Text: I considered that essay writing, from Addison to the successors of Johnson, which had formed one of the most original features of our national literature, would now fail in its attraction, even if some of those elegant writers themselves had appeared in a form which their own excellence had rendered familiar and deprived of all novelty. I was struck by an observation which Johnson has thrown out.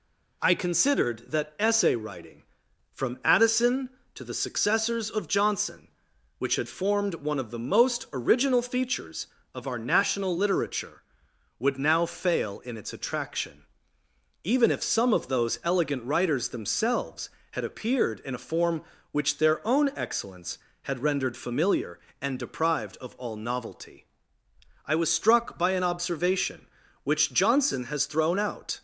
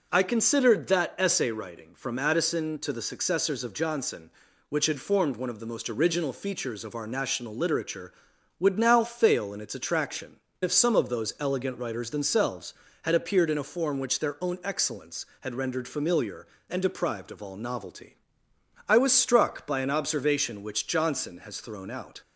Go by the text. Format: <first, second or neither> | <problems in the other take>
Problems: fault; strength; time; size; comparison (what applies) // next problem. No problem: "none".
first | skips "even"; at 10.4 s